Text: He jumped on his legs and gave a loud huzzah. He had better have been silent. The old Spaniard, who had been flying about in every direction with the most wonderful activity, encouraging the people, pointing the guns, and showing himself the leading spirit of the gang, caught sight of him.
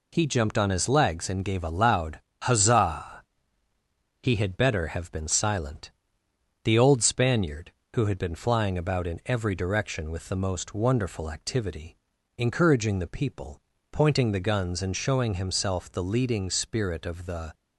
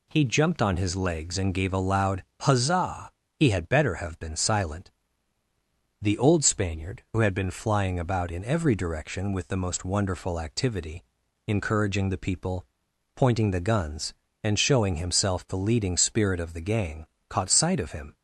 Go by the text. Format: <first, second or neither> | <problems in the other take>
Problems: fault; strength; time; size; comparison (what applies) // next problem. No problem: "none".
second | pauses between "loud" and "huzzah"; slight; at 2.1 s; 0.22 s long; slight in the second // stops before "gang caught sight of him"; at 17.5 s